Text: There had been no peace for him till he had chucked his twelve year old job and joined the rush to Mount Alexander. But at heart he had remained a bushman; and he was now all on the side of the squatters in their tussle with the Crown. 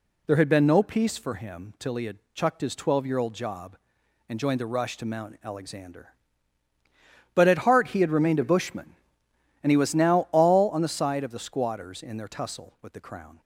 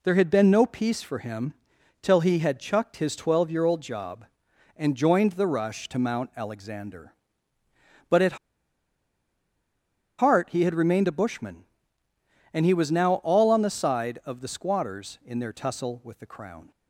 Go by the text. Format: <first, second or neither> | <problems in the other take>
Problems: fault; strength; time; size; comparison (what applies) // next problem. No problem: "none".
first | pauses between "him" and "till"; noticeable; at 1.5 s; 0.50 s long // pauses between "at" and "heart"; strong; at 8.3 s; 1.8 s long